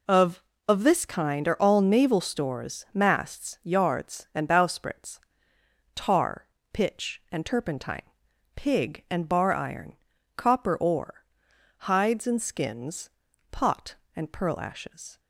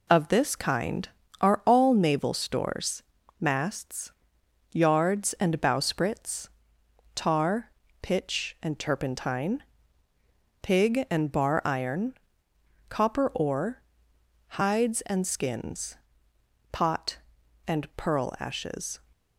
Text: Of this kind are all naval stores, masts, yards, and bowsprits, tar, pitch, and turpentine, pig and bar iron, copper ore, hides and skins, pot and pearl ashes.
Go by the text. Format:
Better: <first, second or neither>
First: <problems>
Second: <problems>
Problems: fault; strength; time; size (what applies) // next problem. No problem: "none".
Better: second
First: says "Of" twice; at 0.6 s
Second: none